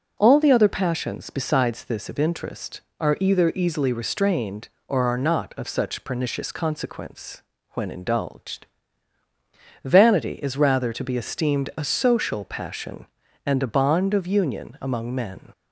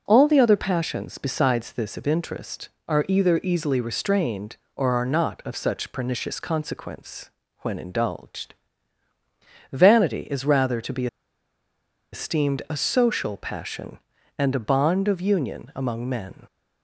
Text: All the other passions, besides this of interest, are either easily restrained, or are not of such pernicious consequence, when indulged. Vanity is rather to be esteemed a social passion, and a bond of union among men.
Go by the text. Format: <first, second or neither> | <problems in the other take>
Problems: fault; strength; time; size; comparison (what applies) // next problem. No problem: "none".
first | pauses between "be" and "esteemed"; at 11.0 s; 1.0 s long